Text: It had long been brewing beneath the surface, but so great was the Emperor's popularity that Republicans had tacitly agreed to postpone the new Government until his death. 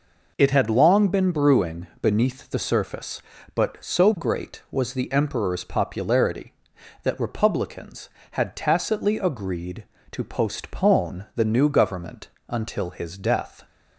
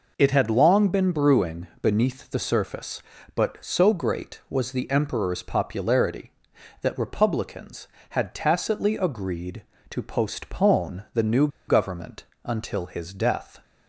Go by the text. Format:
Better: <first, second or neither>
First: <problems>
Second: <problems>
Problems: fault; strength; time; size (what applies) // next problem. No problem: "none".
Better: first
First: pauses between "brewing" and "beneath"; slight; at 1.8 s; 0.16 s long // pauses between "Government" and "until"; slight; at 12.2 s; 0.22 s long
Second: pauses between "brewing" and "beneath"; slight; at 1.6 s; 0.16 s long // pauses between "new" and "Government"; slight; at 11.4 s; 0.20 s long // pauses between "Government" and "until"; slight; at 12.2 s; 0.22 s long